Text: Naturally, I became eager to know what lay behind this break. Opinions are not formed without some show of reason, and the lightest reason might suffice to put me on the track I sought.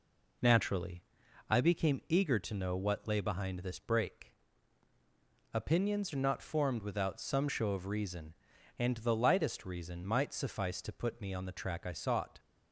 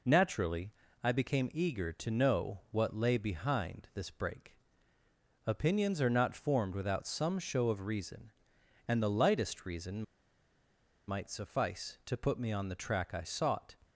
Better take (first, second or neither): first